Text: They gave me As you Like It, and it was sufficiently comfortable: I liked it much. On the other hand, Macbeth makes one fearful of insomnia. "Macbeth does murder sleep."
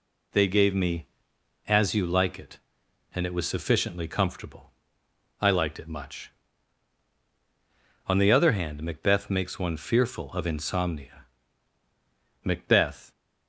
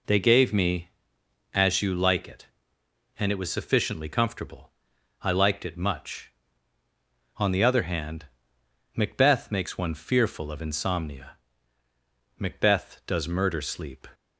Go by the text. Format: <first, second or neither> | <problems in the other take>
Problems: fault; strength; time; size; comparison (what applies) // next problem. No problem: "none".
second | stops before "does murder sleep"; at 13.1 s